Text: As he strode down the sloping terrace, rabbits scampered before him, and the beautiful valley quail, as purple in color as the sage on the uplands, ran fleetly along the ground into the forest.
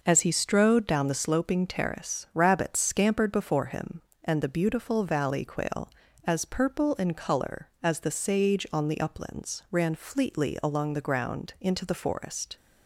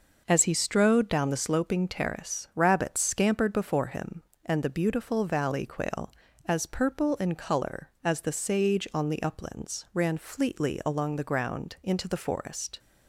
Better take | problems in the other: neither | none

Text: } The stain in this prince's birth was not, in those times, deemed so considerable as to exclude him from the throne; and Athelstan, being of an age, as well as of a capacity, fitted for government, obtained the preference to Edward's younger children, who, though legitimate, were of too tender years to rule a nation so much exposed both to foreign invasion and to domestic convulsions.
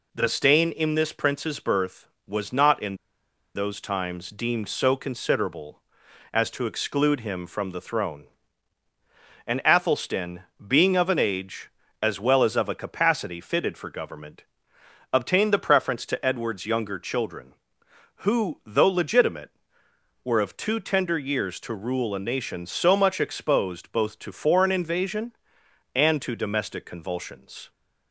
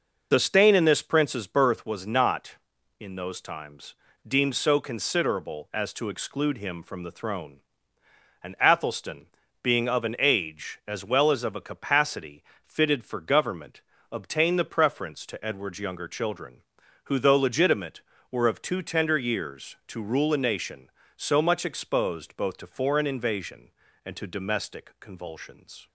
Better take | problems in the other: second | pauses between "in" and "those"; noticeable; at 2.9 s; 0.58 s long

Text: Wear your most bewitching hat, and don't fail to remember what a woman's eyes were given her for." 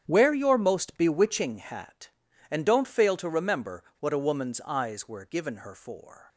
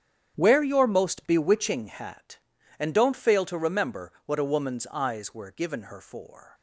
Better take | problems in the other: neither | starts louder than the rest; strong; the same in both // pauses between "remember" and "what"; slight; the same in both

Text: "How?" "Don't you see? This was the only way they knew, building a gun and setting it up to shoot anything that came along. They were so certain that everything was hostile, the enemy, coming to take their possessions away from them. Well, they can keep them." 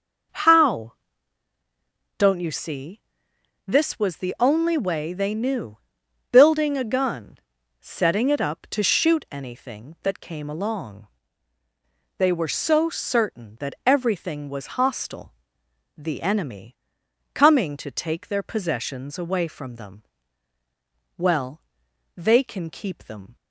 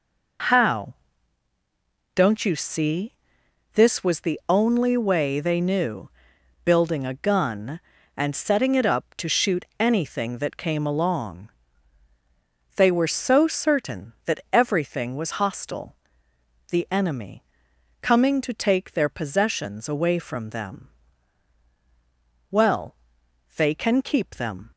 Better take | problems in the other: second | skips "and"; at 7.6 s

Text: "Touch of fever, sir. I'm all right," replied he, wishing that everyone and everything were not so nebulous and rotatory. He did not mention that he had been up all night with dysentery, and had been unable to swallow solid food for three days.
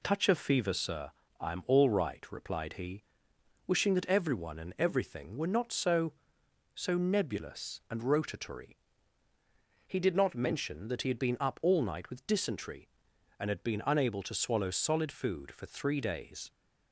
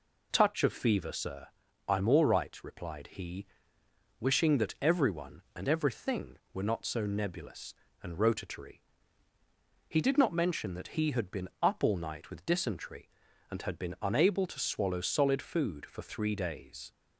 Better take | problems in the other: second | says "so" twice; at 6.7 s

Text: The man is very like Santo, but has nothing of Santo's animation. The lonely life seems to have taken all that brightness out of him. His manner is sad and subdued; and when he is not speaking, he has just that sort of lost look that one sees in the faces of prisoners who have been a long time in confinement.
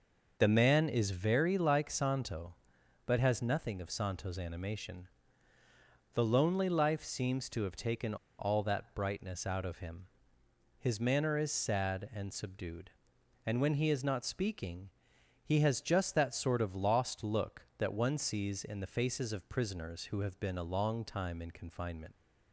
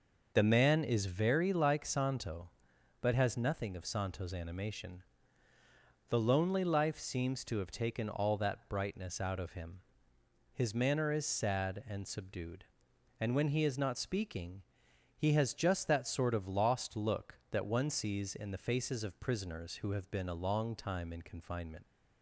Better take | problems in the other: second | pauses between "taken" and "all"; slight; at 8.1 s; 0.23 s long

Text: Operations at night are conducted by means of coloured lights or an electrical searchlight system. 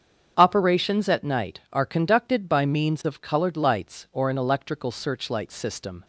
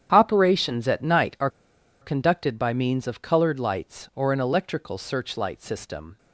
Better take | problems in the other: first | starts louder than the rest; strong; until 1.1 s; 9 dB; strong in the first // pauses between "are" and "conducted"; noticeable; at 1.4 s; 0.52 s long

